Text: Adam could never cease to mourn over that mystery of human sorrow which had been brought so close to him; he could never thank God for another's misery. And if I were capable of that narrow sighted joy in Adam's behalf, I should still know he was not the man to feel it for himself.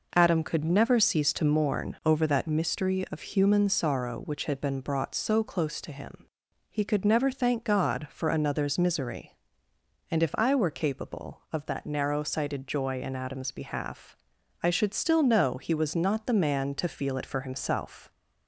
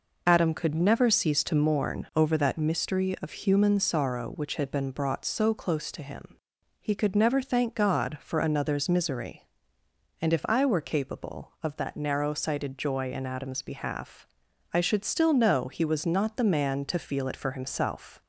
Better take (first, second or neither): first